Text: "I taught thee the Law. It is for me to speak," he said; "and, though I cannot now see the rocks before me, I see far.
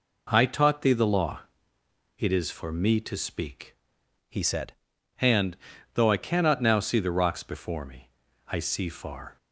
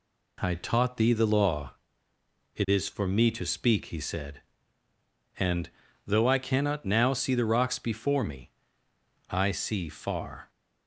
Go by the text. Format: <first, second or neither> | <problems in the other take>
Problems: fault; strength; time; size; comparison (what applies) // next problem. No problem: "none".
second | changes voice from "he" to "said"; from 4.2 to 4.7 s; 0.5 s long